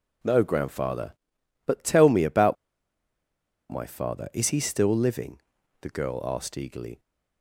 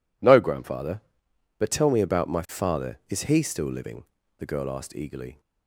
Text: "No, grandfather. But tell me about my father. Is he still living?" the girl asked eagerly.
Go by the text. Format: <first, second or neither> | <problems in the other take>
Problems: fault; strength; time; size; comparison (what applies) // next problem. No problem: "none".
second | pauses between "about" and "my"; at 2.5 s; 1.1 s long